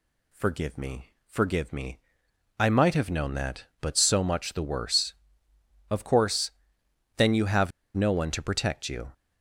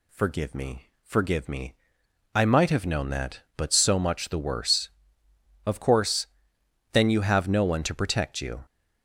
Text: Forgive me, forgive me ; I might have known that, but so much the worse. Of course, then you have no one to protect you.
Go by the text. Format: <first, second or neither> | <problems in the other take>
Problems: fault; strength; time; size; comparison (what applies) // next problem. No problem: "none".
second | pauses between "have" and "no"; slight; at 7.7 s; 0.25 s long